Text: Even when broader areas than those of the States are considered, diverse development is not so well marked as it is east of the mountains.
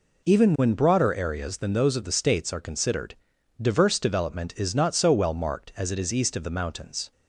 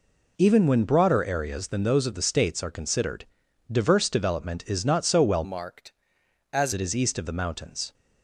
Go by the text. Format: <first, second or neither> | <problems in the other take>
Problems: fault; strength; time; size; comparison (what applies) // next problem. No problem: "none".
first | changes voice from "marked" to "as"; from 5.4 to 6.7 s; 1.3 s long